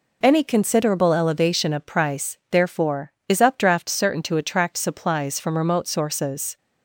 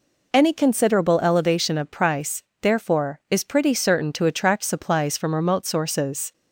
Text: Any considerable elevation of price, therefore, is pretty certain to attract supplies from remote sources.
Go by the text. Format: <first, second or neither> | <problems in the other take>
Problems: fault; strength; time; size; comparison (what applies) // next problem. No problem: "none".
second | says "updraft" for "pretty"; at 3.4 s